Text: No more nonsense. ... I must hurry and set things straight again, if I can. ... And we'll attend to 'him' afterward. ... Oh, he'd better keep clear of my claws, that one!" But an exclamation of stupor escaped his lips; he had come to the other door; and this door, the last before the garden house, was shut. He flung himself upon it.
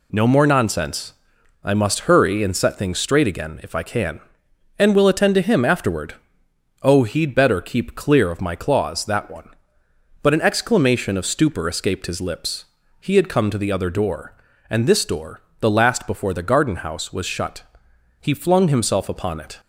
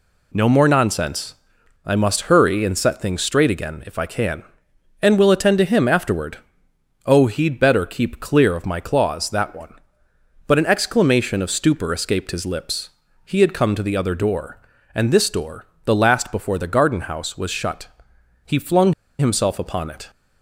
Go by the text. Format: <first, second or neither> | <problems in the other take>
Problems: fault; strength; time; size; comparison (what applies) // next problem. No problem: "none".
first | pauses between "flung" and "himself"; slight; at 18.9 s; 0.26 s long